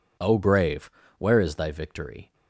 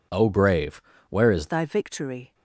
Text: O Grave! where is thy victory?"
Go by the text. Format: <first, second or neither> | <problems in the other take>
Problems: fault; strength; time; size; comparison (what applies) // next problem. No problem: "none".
first | changes voice at "thy"; from 1.4 s on; 0.9 s long